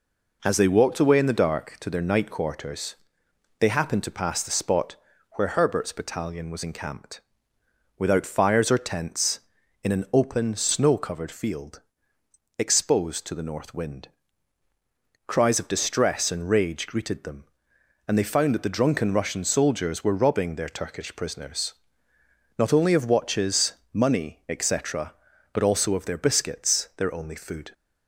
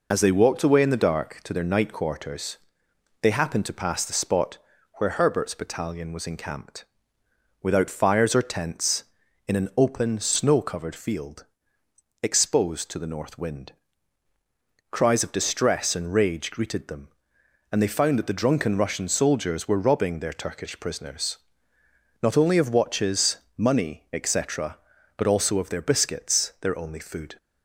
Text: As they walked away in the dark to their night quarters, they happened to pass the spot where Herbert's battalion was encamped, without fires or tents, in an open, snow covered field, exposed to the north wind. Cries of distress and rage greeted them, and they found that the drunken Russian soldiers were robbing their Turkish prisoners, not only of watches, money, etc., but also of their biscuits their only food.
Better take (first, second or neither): first